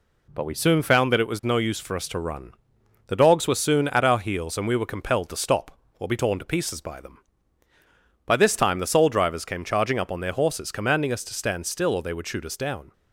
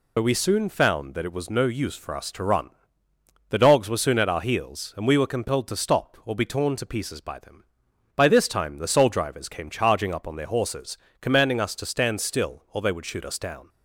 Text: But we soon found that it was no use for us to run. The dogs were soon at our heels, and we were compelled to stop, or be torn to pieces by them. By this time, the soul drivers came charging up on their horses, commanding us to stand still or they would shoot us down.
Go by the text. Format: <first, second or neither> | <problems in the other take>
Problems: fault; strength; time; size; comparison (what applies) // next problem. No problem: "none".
first | loses the start of "But"; at 0.1 s; 50 ms